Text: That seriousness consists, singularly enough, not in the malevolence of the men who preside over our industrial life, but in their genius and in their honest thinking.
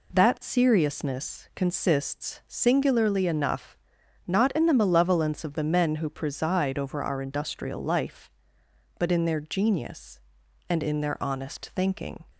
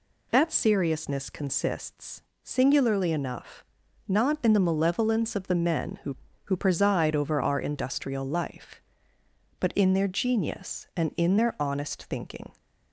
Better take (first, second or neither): first